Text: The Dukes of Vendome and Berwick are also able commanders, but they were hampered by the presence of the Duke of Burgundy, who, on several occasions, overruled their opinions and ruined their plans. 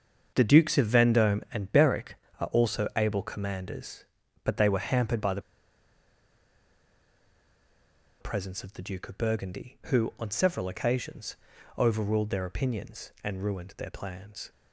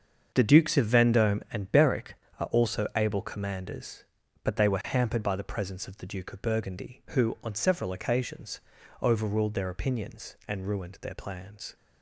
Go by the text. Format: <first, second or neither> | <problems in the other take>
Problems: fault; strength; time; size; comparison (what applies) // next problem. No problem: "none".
second | starts louder than the rest; until 1.3 s; 7 dB; also in the second // pauses between "the" and "presence"; strong; at 5.4 s; 2.7 s long